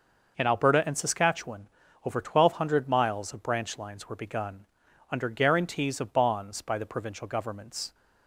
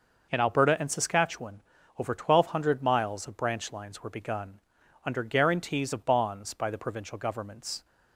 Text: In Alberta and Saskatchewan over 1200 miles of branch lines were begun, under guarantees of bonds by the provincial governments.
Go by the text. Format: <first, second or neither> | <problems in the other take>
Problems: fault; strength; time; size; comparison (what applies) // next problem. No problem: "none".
neither | pauses between "Saskatchewan" and "over"; slight; the same in both